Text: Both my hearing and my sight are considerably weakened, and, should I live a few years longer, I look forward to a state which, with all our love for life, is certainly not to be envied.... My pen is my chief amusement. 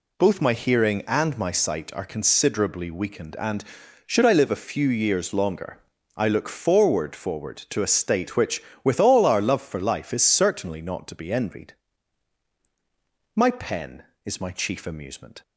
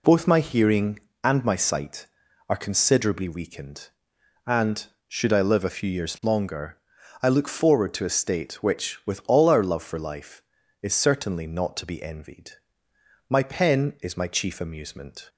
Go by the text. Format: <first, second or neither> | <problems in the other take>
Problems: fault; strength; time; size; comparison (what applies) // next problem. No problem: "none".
second | says "forward" twice; at 7.1 s